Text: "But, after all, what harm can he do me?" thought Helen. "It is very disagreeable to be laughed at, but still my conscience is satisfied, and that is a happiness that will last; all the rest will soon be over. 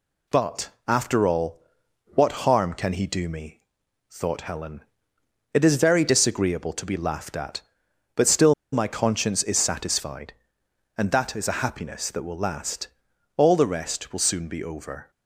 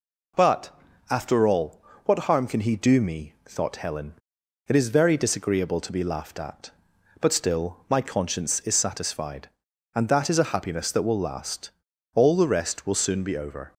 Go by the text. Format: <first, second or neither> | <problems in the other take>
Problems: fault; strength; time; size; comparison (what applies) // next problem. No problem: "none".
second | pauses between "still" and "my"; slight; at 8.5 s; 0.18 s long